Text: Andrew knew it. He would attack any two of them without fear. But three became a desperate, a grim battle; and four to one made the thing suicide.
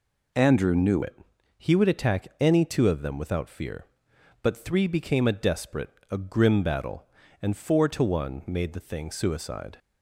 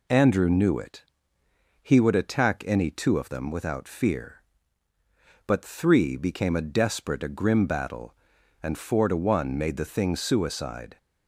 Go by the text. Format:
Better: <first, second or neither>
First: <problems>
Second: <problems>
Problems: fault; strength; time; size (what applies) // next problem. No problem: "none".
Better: second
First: changes voice at "it"; from 1.0 s on; 8.7 s long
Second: none